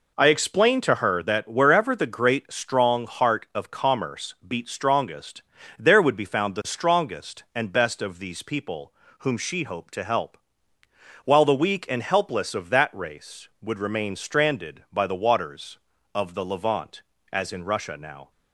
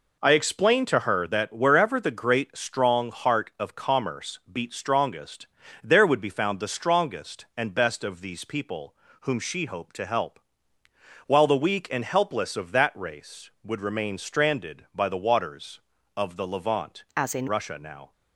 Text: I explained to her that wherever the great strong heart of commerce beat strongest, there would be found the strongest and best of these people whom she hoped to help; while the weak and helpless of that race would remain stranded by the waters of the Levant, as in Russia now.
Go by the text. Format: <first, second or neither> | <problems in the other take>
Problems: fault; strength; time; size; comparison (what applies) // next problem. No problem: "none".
first | pauses between "people" and "whom"; slight; at 8.9 s; 0.28 s long; slight in the first // changes voice from "as" to "in"; from 17.1 to 17.4 s; 0.3 s long